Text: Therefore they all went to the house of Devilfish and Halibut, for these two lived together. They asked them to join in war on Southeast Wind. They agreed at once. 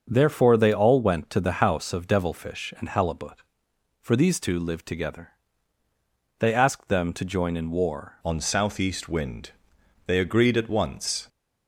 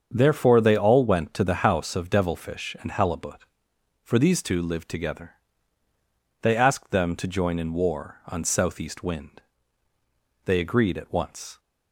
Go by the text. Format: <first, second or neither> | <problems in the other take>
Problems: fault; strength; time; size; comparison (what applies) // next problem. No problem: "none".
second | starts louder than the rest; until 1.1 s; 6.5 dB; also in the second // changes voice at "on"; from 8.2 s on; 3.0 s long